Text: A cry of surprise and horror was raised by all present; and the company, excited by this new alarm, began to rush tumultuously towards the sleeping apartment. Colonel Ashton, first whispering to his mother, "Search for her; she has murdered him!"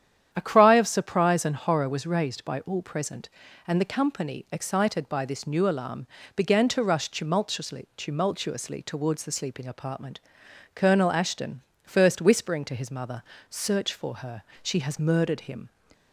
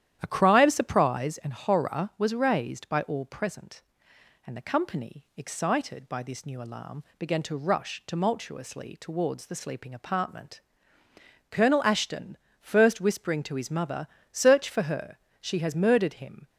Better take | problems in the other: second | starts louder than the rest; strong; until 1.3 s; 9.5 dB; strong in the second // says "tumultuously" twice; at 7.9 s

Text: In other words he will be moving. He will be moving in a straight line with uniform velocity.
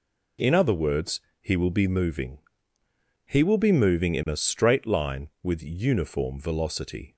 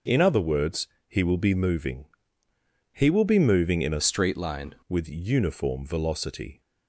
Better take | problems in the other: first | pauses between "words" and "he"; slight; at 0.8 s; 0.22 s long; slight in the first // changes voice from "straight" to "line"; from 4.0 to 4.7 s; 0.7 s long

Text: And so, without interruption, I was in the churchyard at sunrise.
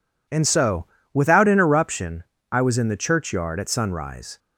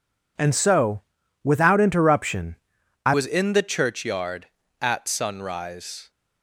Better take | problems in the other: first | changes voice at "was"; from 3.1 s on; 3.0 s long

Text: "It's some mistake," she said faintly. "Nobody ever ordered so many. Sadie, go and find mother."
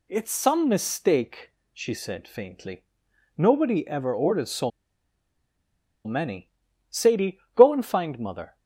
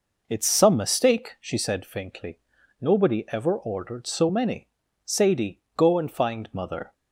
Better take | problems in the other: second | pauses between "so" and "many"; strong; at 4.6 s; 1.3 s long

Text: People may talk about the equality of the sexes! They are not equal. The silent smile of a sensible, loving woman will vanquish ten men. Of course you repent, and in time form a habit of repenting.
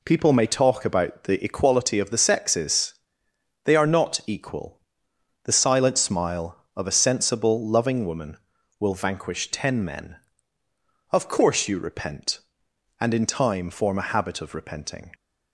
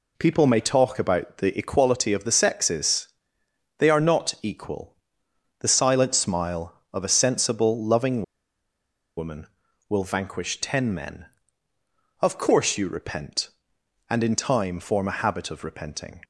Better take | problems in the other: first | pauses between "loving" and "woman"; noticeable; at 8.2 s; 0.94 s long

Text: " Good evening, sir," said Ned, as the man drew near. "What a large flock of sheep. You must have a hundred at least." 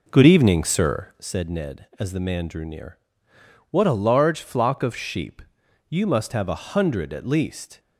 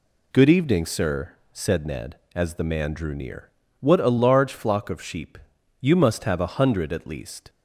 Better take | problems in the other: second | starts louder than the rest; noticeable; until 1.3 s; 4 dB

